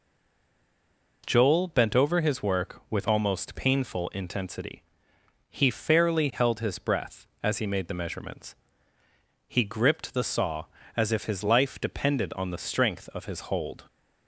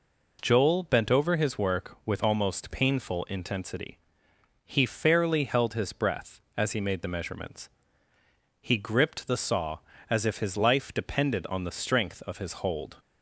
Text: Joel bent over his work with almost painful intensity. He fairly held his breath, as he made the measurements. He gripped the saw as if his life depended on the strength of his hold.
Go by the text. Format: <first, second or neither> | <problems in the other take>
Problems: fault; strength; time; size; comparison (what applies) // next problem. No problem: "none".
second | stays silent before the first word; noticeable; until 1.2 s; 1.2 s long